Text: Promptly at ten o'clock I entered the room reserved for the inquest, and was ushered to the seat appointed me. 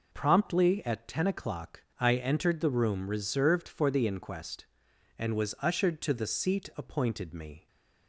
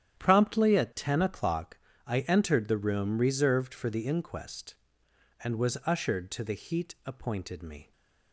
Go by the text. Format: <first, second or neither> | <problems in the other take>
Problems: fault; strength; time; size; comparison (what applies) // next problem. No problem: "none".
first | starts louder than the rest; strong; until 1.2 s; 10 dB // pauses between "o'clock" and "I"; slight; at 1.7 s; 0.28 s long; slight in the first // says "heat" for "seat"; at 6.5 s